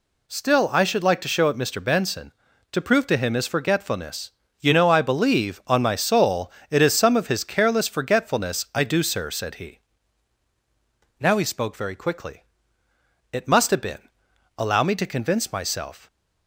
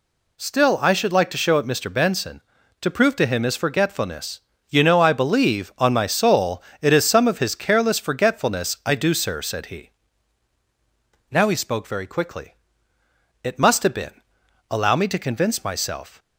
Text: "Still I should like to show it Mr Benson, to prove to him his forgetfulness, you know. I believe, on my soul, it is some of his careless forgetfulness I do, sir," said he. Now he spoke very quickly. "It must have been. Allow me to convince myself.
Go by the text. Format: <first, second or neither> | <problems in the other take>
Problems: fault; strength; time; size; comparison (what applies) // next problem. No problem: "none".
neither | none